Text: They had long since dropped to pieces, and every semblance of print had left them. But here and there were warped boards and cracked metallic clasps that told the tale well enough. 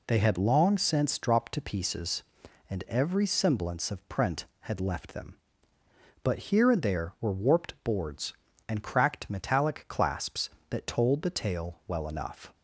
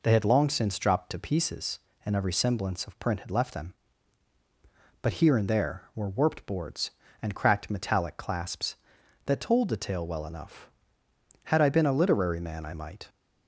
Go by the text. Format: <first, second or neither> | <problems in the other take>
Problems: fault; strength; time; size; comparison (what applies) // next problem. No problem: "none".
first | goes on to say "Had I been a literary man I might"; from 11.4 s on; 1.6 s long